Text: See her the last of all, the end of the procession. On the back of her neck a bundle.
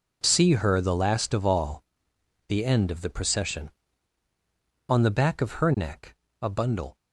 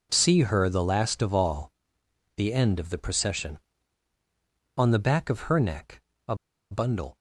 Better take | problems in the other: first | pauses between "neck" and "a"; slight; at 6.0 s; 0.24 s long; slight in the first // pauses between "a" and "bundle"; at 6.3 s; 0.36 s long

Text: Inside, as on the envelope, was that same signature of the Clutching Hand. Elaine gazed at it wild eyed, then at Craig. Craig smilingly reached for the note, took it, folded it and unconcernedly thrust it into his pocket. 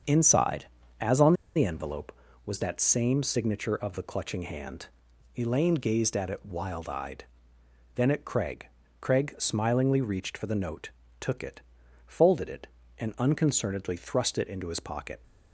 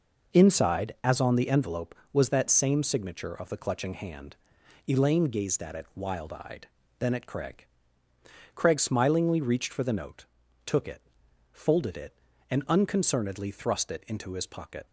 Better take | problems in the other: second | starts louder than the rest; strong; until 1.6 s; 7 dB // pauses between "on" and "the"; slight; at 1.3 s; 0.22 s long

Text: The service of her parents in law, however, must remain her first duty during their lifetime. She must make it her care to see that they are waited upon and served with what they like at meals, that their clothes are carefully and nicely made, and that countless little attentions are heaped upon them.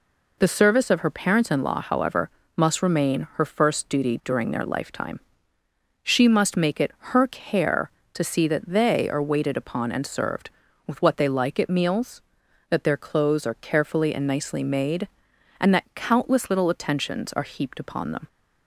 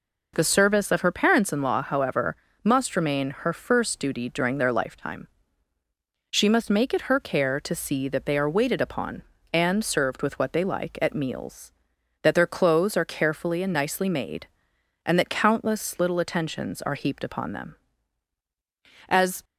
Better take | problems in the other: first | goes on to say "As"; slight; from 19.0 s on; 0.34 s long

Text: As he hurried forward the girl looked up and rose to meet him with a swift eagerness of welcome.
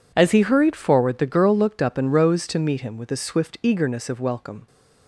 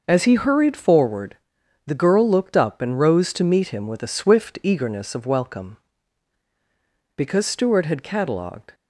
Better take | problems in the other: first | pauses between "forward" and "the"; noticeable; at 1.3 s; 0.50 s long // goes on to say "Because Stuart had catalogued"; from 7.1 s on; 1.5 s long

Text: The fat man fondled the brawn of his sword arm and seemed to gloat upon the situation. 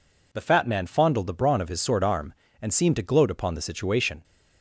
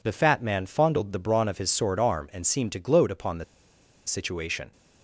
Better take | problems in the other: first | pauses between "the" and "situation"; noticeable; at 3.4 s; 0.63 s long

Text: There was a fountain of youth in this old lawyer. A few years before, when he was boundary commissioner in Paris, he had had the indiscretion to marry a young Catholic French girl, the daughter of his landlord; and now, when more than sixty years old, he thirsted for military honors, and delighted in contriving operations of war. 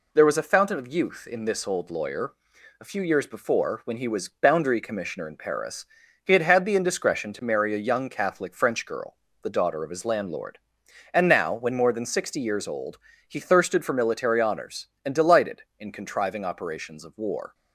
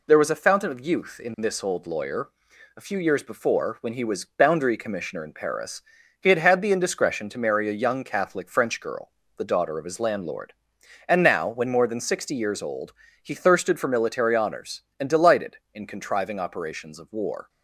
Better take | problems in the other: neither | none

